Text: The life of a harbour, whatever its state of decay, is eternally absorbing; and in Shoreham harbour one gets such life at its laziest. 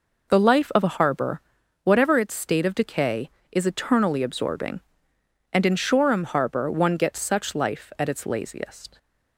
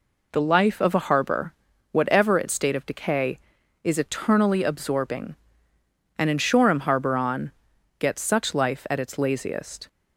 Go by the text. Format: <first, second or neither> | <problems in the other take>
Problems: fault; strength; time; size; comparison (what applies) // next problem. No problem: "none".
first | says "on" for "one"; at 7.1 s